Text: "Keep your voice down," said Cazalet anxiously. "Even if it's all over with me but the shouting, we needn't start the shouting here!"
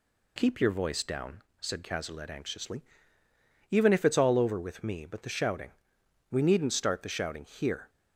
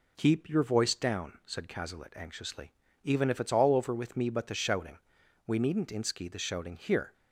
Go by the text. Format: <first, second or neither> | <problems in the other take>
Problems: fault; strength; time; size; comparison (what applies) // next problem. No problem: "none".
first | says "inski" for "start"; at 5.9 s